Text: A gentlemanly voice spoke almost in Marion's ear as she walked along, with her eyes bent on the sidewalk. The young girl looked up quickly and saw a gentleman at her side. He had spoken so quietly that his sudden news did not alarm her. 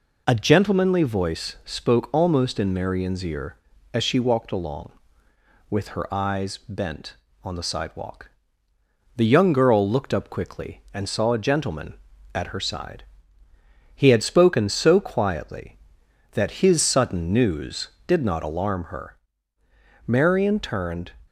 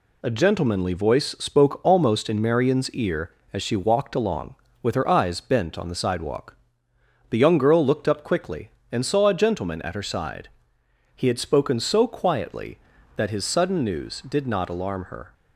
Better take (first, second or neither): second